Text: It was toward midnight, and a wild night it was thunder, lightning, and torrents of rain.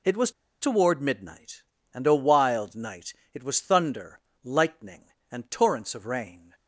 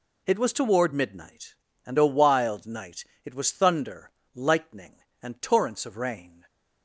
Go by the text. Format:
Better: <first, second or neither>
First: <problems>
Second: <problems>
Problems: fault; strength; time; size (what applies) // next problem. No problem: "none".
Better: second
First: pauses between "was" and "toward"; slight; at 0.3 s; 0.29 s long // pauses between "night" and "it"; slight; at 3.1 s; 0.20 s long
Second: pauses between "night" and "it"; slight; at 3.0 s; 0.20 s long